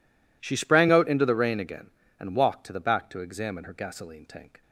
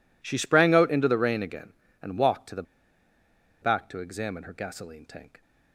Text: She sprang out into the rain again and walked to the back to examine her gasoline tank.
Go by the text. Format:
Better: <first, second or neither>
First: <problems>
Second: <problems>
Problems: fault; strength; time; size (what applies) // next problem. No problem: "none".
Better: first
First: none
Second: pauses between "the" and "back"; at 2.6 s; 0.99 s long